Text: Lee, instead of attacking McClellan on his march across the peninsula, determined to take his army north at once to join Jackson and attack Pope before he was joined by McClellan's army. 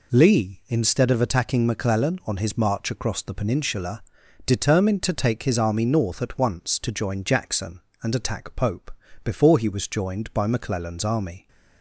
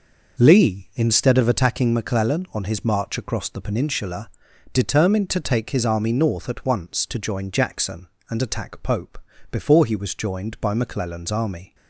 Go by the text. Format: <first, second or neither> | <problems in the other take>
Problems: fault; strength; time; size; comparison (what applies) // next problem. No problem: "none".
first | starts louder than the rest; noticeable; until 1.9 s; 5.5 dB // pauses between "Pope" and "before"; slight; at 9.1 s; 0.32 s long; slight in the first